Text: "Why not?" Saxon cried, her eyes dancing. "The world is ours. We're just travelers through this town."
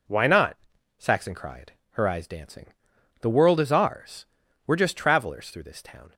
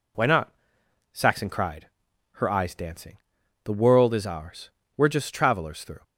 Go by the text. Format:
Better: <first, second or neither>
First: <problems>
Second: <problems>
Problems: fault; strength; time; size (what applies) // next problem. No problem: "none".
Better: first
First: none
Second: stops before "this town"; at 6.0 s